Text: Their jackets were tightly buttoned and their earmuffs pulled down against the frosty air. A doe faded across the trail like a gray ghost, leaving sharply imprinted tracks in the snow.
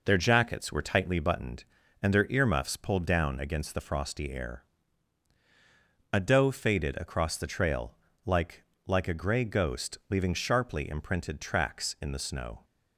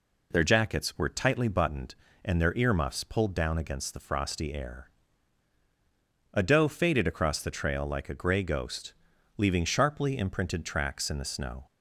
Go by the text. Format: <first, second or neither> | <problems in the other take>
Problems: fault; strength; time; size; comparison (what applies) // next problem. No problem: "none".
second | pauses between "trail" and "like"; slight; at 7.9 s; 0.32 s long // says "like" twice; at 8.8 s